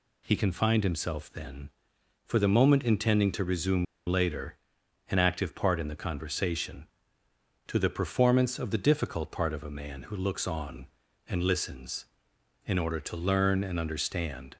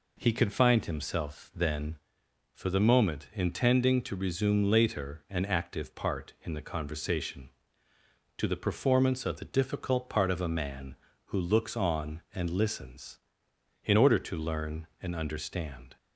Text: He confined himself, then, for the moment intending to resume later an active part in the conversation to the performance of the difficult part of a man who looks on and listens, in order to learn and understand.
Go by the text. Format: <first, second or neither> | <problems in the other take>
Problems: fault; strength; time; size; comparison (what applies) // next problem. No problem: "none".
second | pauses between "resume" and "later"; slight; at 3.8 s; 0.22 s long // pauses between "later" and "an"; noticeable; at 4.5 s; 0.54 s long